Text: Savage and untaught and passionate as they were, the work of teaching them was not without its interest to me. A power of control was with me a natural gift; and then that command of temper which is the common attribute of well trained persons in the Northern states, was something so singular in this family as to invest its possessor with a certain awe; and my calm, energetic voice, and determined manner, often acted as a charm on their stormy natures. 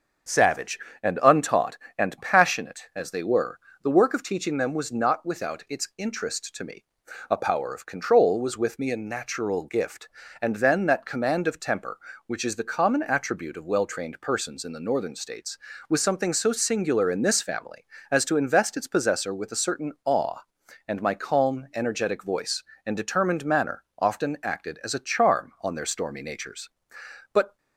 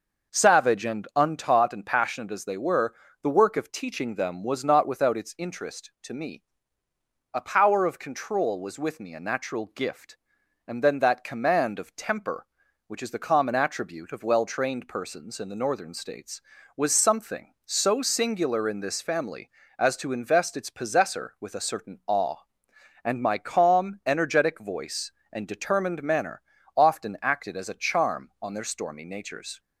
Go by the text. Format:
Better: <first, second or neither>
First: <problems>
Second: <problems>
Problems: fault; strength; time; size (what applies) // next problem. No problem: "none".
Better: second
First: starts louder than the rest; strong; until 1.5 s; 7 dB // goes on to say "But"; slight; from 27.3 s on; 0.26 s long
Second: none